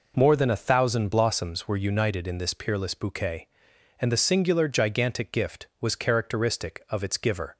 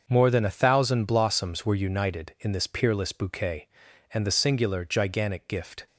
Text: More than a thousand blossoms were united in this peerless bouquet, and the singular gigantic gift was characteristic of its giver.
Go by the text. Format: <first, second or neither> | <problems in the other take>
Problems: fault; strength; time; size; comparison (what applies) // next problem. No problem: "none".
first | starts louder than the rest; until 1.0 s; 6.5 dB // stops before "was characteristic of its giver"; at 5.8 s